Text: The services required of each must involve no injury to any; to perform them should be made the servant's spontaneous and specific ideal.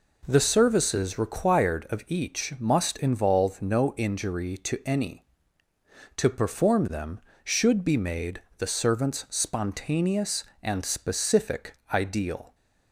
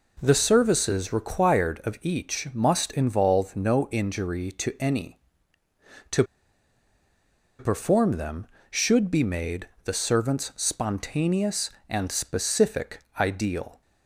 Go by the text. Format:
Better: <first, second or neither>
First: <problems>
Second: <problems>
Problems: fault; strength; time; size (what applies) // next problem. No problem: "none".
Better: first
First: pauses between "made" and "the"; slight; at 8.4 s; 0.16 s long // pauses between "specific" and "ideal"; slight; at 11.7 s; 0.18 s long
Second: pauses between "to" and "perform"; strong; at 6.2 s; 1.3 s long // pauses between "made" and "the"; slight; at 9.6 s; 0.16 s long // pauses between "specific" and "ideal"; slight; at 13.0 s; 0.18 s long